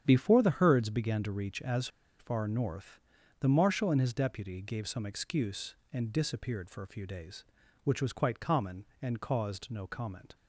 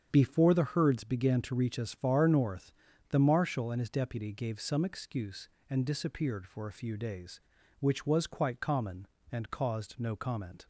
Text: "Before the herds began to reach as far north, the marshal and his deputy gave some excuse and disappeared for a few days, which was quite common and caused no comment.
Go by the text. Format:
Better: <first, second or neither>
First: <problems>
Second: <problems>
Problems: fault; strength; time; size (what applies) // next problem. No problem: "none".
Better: second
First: starts louder than the rest; strong; until 1.0 s; 8.5 dB // pauses between "as" and "far"; slight; at 1.8 s; 0.31 s long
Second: starts louder than the rest; strong; until 1.1 s; 7.5 dB